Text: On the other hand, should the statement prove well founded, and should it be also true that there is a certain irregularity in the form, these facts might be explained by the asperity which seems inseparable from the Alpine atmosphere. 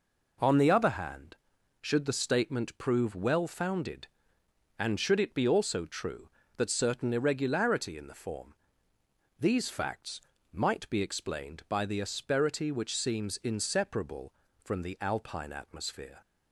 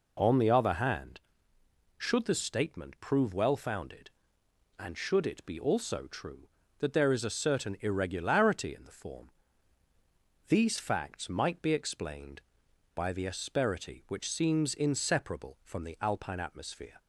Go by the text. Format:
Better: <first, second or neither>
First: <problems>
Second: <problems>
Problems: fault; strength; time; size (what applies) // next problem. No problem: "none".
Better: second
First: skips "there is a"; at 6.6 s // pauses between "facts" and "might"; slight; at 10.2 s; 0.32 s long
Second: none